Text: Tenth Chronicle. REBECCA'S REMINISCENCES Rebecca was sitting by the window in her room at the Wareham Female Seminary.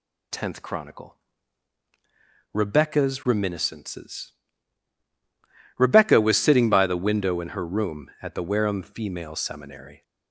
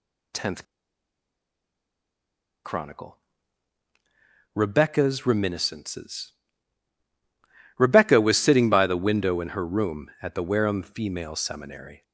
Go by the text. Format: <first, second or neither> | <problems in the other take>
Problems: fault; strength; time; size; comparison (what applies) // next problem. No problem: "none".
first | pauses between "Tenth" and "Chronicle"; strong; at 0.6 s; 2.0 s long // pauses between "REMINISCENCES" and "Rebecca"; strong; at 6.3 s; 1.4 s long; strong in the first